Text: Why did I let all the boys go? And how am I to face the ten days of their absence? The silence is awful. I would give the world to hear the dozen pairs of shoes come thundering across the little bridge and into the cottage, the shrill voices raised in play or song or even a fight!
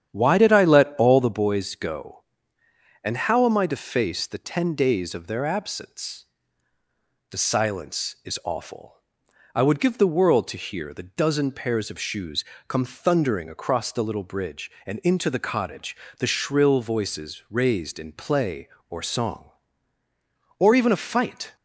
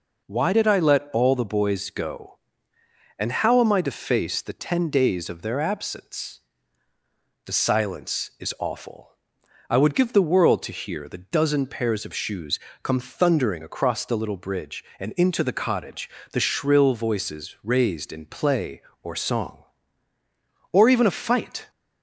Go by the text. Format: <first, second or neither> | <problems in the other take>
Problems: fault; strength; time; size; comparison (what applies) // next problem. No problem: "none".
second | starts louder than the rest; strong; until 1.5 s; 9 dB // pauses between "shoes" and "come"; slight; at 12.4 s; 0.24 s long; slight in the second